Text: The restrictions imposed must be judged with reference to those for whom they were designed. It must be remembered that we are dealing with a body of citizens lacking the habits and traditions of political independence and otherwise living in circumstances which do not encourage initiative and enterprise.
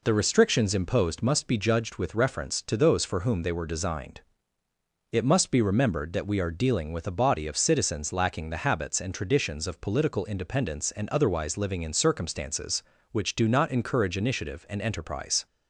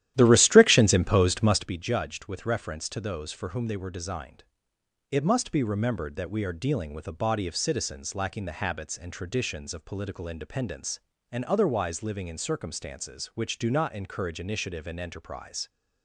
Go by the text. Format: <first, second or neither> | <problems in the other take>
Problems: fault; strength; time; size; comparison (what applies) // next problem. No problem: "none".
first | starts louder than the rest; strong; until 1.8 s; 12.5 dB